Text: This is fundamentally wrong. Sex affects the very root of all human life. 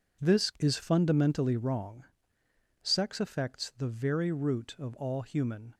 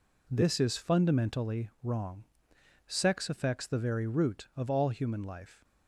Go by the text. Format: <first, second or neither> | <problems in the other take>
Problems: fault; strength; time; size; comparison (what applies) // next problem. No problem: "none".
second | stops before "life"; at 5.7 s